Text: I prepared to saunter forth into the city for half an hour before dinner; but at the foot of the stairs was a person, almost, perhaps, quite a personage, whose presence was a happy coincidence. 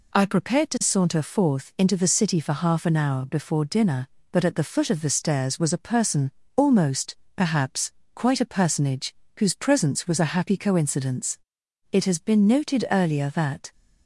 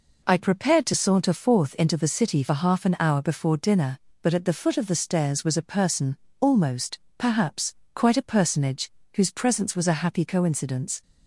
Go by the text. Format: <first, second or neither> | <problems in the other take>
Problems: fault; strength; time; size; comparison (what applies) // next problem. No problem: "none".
second | goes on to say "It has been noted earlier that"; strong; from 11.9 s on; 1.7 s long